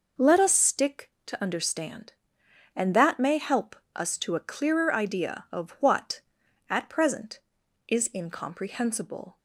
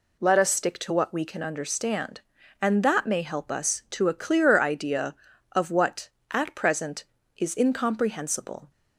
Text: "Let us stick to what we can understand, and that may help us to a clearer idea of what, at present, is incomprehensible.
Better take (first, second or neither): second